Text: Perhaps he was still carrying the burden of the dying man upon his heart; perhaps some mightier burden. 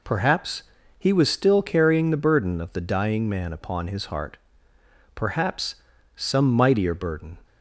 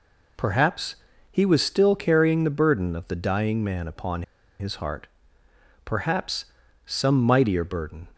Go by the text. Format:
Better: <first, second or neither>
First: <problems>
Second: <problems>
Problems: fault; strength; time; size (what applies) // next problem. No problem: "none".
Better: first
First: pauses between "Perhaps" and "he"; slight; at 0.6 s; 0.34 s long // pauses between "perhaps" and "some"; at 5.7 s; 0.40 s long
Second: pauses between "Perhaps" and "he"; slight; at 0.9 s; 0.34 s long // pauses between "upon" and "his"; at 4.2 s; 0.36 s long // pauses between "perhaps" and "some"; at 6.4 s; 0.40 s long